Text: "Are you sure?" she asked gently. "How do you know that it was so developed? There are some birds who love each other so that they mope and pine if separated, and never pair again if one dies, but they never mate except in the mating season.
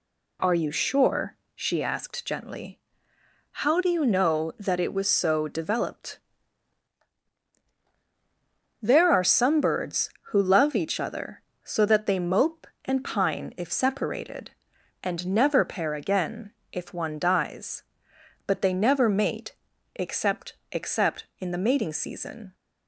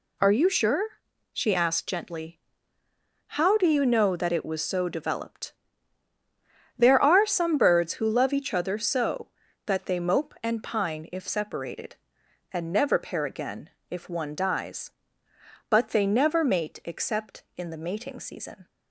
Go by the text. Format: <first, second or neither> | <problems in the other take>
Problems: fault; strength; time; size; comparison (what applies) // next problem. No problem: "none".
second | pauses between "again" and "if"; slight; at 16.5 s; 0.20 s long; slight in the second // pauses between "mate" and "except"; at 19.5 s; 0.42 s long // says "except" twice; at 20.7 s